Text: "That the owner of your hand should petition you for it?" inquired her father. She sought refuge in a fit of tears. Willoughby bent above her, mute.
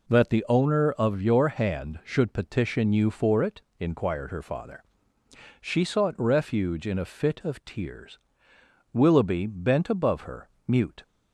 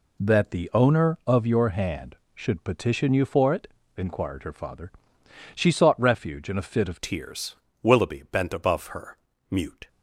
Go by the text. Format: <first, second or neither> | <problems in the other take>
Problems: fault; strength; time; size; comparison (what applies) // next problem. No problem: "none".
first | changes voice at "tears"; from 7.0 s on; 2.8 s long